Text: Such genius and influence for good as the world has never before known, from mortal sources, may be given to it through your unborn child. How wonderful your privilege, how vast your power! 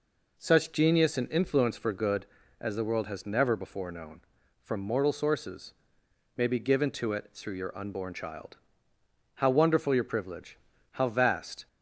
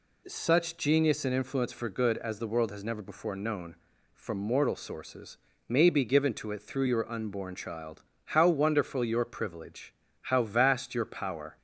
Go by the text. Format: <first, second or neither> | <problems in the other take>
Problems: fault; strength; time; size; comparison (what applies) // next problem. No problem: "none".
second | stops before "your power"; at 11.6 s